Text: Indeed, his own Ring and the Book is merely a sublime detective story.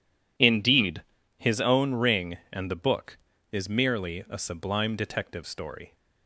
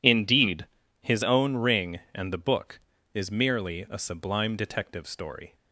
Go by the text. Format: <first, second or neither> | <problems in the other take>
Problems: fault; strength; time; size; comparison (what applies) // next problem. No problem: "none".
neither | none